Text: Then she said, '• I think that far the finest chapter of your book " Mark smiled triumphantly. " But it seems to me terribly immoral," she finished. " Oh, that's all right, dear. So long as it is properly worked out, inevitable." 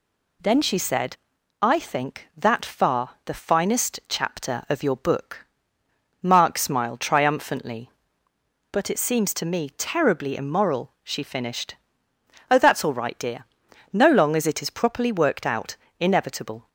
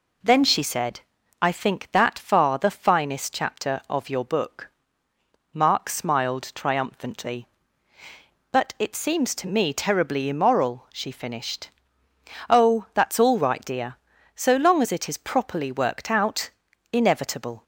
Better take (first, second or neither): second